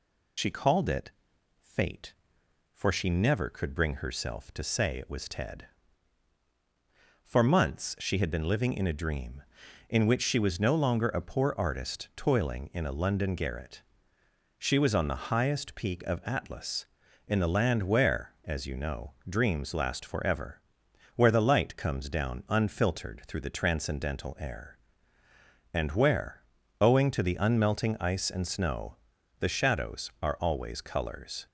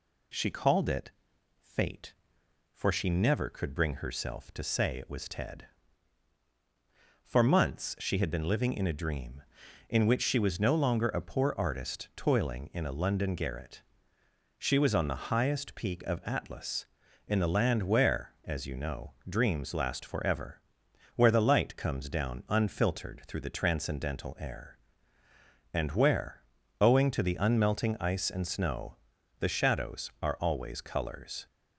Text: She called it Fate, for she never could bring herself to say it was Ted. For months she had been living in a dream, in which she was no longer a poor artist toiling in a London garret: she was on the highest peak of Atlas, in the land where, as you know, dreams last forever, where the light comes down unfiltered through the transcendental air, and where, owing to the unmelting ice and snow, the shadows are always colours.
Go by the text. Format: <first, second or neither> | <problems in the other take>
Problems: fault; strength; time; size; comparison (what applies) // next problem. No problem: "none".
second | loses the start of "She"; at 0.3 s; 65 ms // pauses between "it" and "Fate"; noticeable; at 1.1 s; 0.50 s long; noticeable in the second